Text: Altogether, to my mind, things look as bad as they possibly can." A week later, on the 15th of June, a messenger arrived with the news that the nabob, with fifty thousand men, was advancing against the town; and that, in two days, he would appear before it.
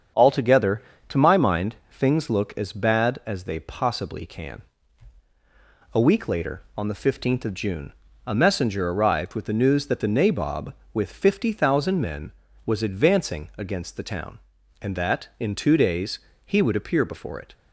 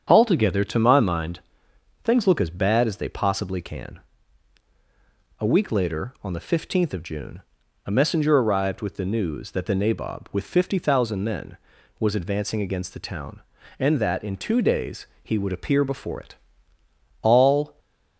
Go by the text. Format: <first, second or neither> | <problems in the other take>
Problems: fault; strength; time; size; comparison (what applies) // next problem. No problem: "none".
first | starts louder than the rest; strong; until 1.0 s; 8 dB; strong in the first // goes on to say "All"; from 17.2 s on; 0.58 s long